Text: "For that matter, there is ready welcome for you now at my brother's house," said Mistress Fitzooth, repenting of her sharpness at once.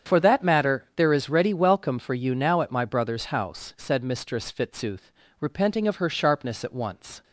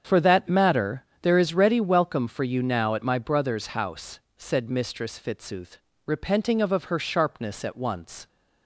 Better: first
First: starts louder than the rest; strong; until 1.1 s; 8 dB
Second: starts louder than the rest; strong; until 1.2 s; 7.5 dB // says "of" twice; at 6.7 s

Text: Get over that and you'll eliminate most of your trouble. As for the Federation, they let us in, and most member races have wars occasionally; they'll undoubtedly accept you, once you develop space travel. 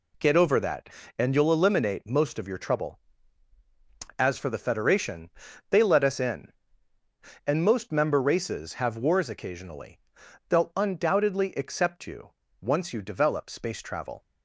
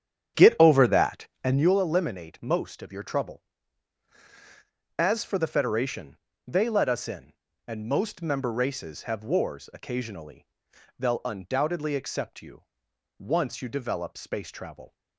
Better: first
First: none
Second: starts louder than the rest; strong; until 1.8 s; 9 dB

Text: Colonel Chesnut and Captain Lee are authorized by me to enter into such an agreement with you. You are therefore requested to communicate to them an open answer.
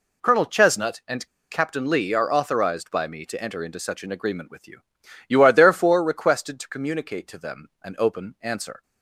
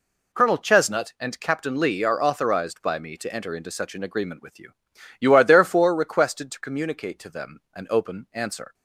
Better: second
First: pauses between "and" and "Captain"; slight; at 1.2 s; 0.24 s long // pauses between "them" and "an"; slight; at 7.6 s; 0.16 s long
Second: pauses between "them" and "an"; slight; at 7.5 s; 0.16 s long

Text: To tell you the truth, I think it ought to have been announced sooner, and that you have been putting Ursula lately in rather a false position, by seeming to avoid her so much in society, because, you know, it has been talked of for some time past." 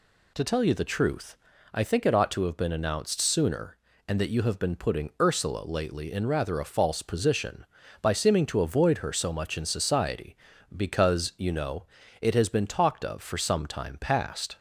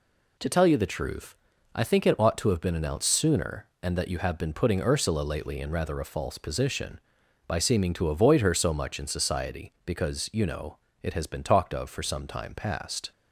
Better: neither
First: none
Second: none

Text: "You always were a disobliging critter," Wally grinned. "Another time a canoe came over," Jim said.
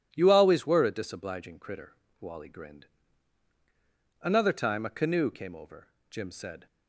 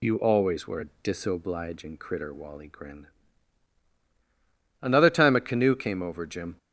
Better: first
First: none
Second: stops before "said"; at 6.5 s

